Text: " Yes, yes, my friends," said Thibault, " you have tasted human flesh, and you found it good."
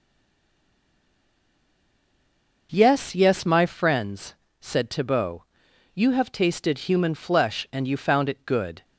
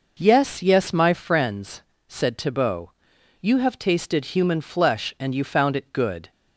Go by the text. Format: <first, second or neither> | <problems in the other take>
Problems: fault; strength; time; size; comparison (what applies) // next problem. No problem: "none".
second | stays silent before the first word; strong; until 2.7 s; 2.7 s long